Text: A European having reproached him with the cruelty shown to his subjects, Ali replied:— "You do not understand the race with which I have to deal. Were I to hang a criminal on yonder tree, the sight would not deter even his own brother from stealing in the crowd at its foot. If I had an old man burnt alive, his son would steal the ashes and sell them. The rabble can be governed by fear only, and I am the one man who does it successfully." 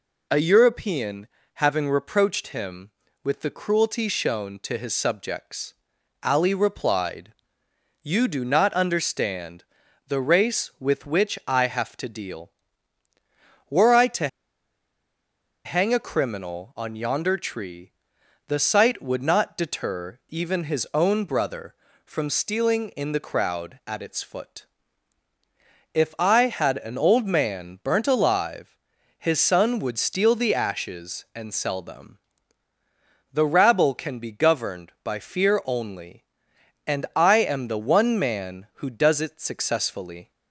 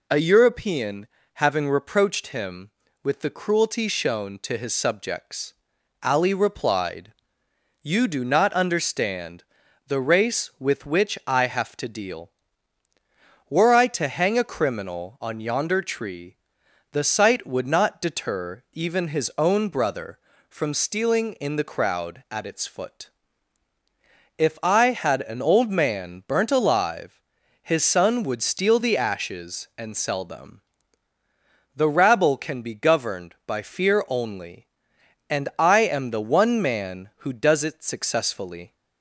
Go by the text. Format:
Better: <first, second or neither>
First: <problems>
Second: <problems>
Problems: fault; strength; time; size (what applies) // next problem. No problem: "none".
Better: second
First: pauses between "European" and "having"; slight; at 1.2 s; 0.28 s long // pauses between "understand" and "the"; at 9.6 s; 0.44 s long // pauses between "to" and "hang"; strong; at 14.2 s; 1.3 s long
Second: pauses between "European" and "having"; slight; at 1.0 s; 0.28 s long // pauses between "understand" and "the"; at 9.4 s; 0.44 s long